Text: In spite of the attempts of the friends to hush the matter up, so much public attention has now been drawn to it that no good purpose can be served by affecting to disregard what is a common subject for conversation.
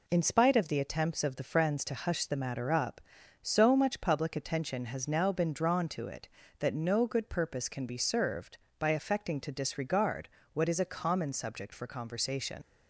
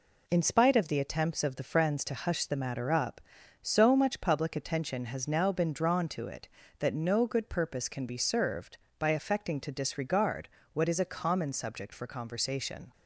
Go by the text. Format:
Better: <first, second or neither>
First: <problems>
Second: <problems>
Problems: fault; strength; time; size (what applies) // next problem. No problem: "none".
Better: second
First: pauses between "disregard" and "what"; slight; at 10.2 s; 0.24 s long // leaves "conversation" unfinished; at 12.6 s; 105 ms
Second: pauses between "disregard" and "what"; slight; at 10.4 s; 0.24 s long